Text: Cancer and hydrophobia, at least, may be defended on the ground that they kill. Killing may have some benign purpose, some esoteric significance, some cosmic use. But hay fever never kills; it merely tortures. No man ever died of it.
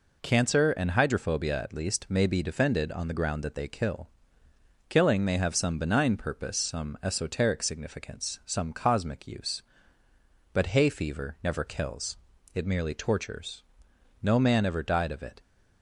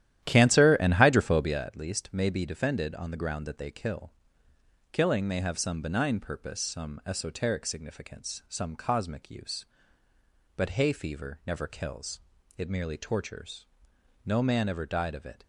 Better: first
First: none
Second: starts louder than the rest; strong; until 1.6 s; 12 dB

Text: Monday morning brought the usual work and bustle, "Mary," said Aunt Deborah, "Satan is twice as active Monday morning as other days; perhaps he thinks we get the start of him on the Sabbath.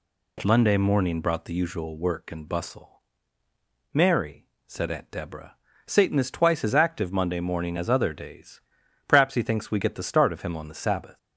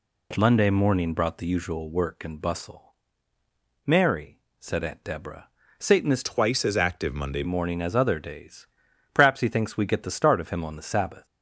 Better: first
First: none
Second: changes voice from "twice" to "Monday"; from 6.2 to 7.4 s; 1.2 s long

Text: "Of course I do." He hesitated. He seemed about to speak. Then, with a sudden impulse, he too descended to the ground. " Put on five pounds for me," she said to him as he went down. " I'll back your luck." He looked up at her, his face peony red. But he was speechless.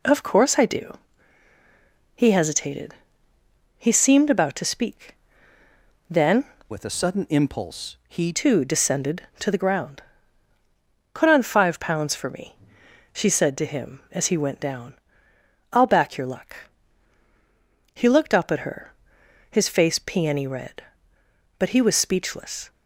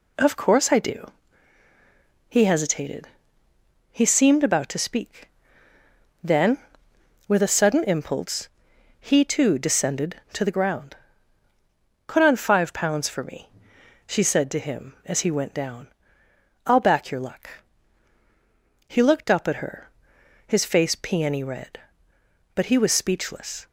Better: second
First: changes voice from "with" to "he"; from 6.7 to 8.3 s; 1.6 s long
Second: none

